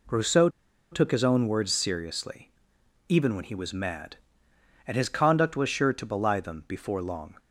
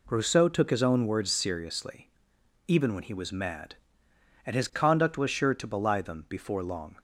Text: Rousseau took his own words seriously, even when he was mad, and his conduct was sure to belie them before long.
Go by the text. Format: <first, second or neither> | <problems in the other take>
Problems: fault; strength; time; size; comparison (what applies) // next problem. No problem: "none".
second | pauses between "Rousseau" and "took"; at 0.4 s; 0.43 s long